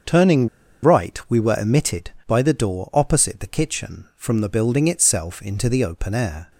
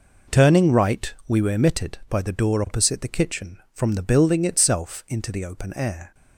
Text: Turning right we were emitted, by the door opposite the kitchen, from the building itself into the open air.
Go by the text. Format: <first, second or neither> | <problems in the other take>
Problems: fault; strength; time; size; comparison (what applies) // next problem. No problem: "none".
second | starts louder than the rest; until 1.5 s; 6.5 dB // pauses between "Turning" and "right"; slight; at 0.4 s; 0.34 s long